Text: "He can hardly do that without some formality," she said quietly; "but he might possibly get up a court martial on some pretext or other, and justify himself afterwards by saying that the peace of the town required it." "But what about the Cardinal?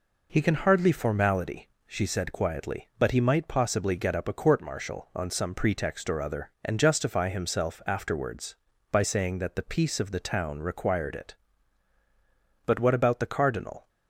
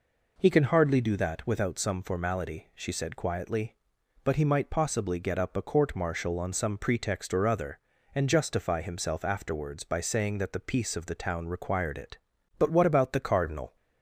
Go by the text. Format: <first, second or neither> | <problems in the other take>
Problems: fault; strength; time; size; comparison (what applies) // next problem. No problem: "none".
second | skips "do that without some"; at 0.9 s